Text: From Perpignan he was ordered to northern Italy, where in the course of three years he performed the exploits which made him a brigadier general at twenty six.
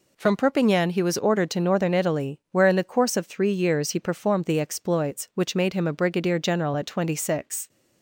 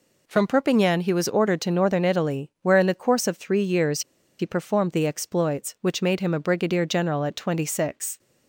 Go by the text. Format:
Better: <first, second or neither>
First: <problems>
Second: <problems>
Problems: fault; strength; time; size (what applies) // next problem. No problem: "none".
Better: first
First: none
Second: pauses between "years" and "he"; at 4.0 s; 0.38 s long